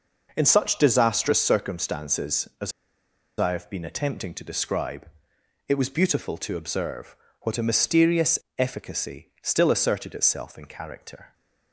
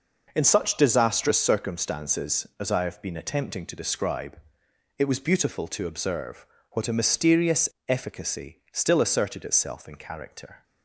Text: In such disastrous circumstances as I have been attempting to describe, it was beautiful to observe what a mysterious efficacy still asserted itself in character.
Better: second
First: pauses between "as" and "I"; noticeable; at 2.7 s; 0.67 s long // pauses between "observe" and "what"; slight; at 7.1 s; 0.26 s long // pauses between "mysterious" and "efficacy"; slight; at 8.3 s; 0.18 s long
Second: pauses between "observe" and "what"; slight; at 6.4 s; 0.26 s long // pauses between "mysterious" and "efficacy"; slight; at 7.6 s; 0.18 s long

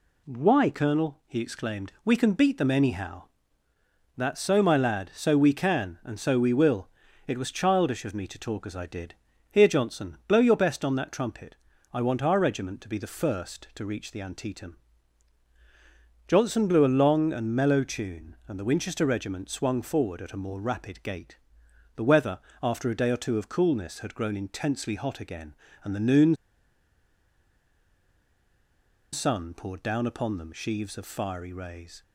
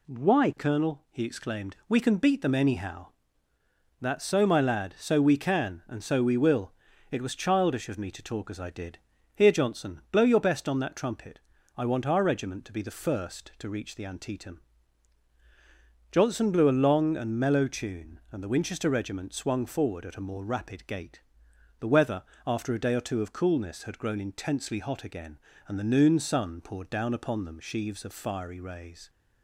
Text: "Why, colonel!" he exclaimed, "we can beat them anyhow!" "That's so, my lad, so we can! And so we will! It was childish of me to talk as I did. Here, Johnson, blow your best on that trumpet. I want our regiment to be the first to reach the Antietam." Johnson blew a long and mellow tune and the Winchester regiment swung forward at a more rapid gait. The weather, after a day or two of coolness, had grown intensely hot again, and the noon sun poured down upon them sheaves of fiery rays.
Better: second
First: pauses between "noon" and "sun"; strong; at 26.3 s; 2.7 s long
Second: none

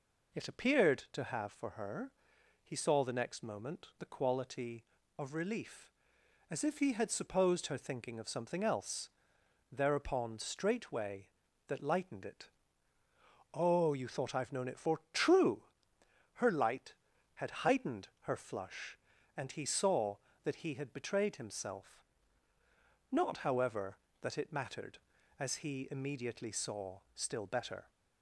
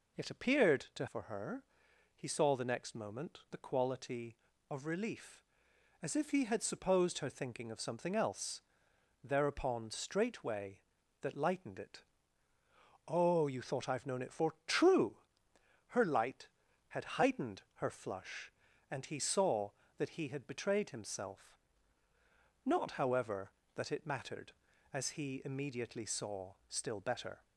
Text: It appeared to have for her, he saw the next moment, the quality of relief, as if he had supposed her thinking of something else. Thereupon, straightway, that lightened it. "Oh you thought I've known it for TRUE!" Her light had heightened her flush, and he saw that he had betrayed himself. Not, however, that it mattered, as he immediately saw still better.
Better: first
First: none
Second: skips "have"; at 1.0 s

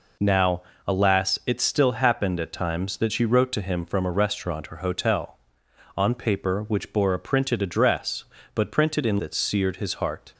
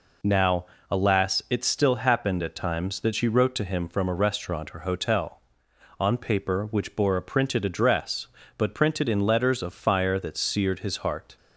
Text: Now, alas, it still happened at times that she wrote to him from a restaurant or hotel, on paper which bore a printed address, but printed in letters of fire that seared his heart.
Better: second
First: skips "letters of fire"; at 9.1 s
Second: none

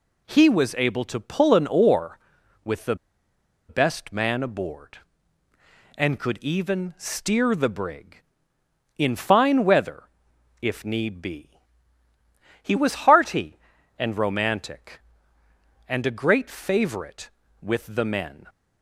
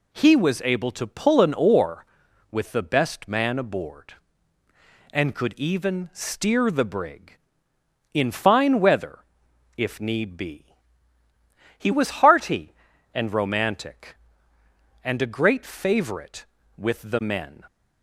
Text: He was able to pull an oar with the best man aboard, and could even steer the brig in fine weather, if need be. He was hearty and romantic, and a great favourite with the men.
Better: second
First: pauses between "the" and "best"; noticeable; at 2.9 s; 0.73 s long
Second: none

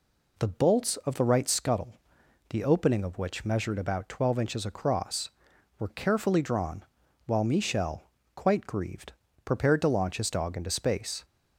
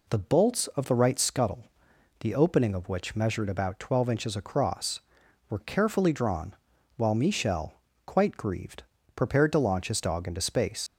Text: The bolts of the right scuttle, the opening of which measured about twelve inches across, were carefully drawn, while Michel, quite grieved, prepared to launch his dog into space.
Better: first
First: none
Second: leaves "space" unfinished; at 10.8 s; 85 ms

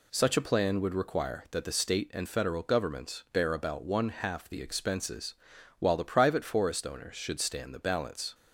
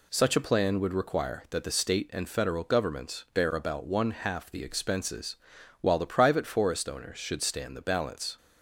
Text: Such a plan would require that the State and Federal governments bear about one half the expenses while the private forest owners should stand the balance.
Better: neither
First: pauses between "expenses" and "while"; at 5.3 s; 0.44 s long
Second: pauses between "expenses" and "while"; at 5.3 s; 0.44 s long

